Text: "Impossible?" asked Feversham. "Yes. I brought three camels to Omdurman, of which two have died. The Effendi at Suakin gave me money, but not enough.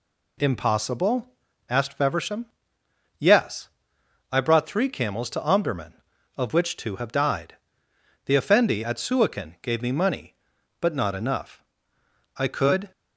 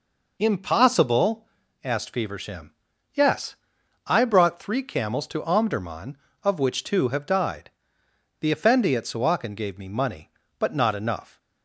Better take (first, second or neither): second